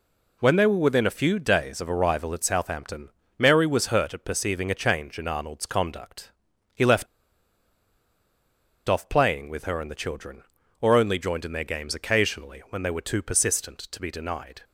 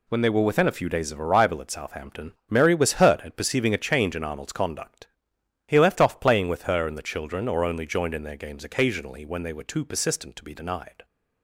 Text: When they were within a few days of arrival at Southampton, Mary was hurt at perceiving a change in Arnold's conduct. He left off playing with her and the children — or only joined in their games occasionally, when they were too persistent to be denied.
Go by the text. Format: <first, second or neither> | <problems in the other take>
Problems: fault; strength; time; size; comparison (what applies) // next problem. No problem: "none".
second | pauses between "left" and "off"; strong; at 7.0 s; 1.8 s long